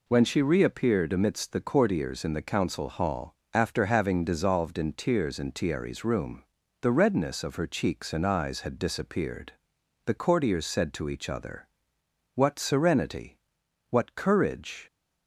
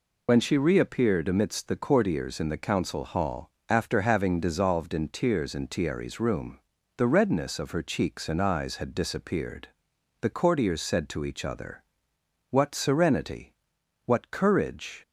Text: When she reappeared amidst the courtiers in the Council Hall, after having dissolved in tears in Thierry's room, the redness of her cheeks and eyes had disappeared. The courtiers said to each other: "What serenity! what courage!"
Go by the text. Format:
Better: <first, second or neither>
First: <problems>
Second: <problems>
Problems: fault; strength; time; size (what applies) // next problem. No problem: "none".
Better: first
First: none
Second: loses the start of "When"; at 0.2 s; 45 ms